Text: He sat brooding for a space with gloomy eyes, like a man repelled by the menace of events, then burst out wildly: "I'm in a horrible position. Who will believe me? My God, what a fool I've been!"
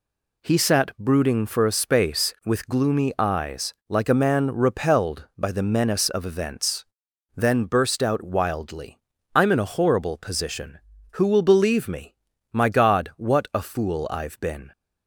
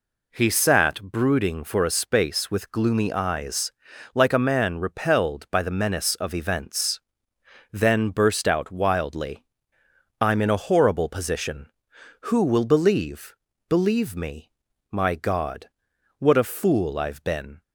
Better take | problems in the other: first | says "believe" twice; at 13.6 s

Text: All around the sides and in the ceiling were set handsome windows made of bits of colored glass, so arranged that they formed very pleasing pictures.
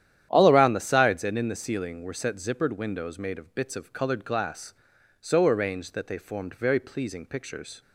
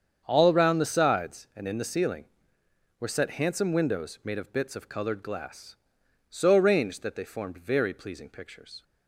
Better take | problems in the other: second | starts louder than the rest; strong; until 1.3 s; 10.5 dB; strong in the second // says "zippered" for "handsome"; at 2.3 s

